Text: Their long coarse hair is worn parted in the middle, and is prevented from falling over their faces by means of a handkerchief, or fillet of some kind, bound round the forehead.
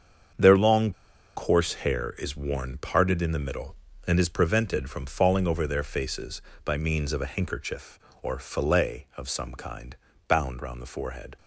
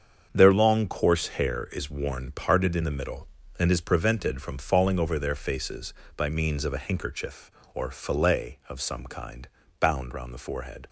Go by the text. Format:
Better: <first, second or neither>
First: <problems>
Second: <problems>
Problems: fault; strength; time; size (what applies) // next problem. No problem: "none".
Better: second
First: starts louder than the rest; strong; until 1.7 s; 7 dB // pauses between "long" and "coarse"; at 0.9 s; 0.44 s long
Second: starts louder than the rest; strong; until 1.3 s; 7 dB